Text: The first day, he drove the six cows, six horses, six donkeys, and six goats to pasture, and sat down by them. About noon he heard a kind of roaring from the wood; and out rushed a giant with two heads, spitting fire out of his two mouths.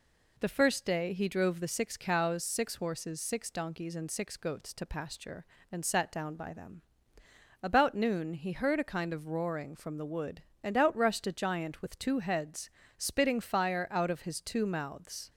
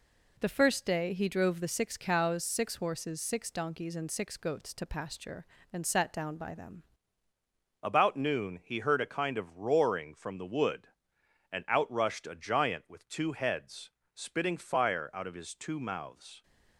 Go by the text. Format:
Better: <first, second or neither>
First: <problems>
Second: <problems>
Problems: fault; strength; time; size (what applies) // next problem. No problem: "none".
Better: first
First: none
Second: changes voice at "About"; from 7.8 s on; 8.6 s long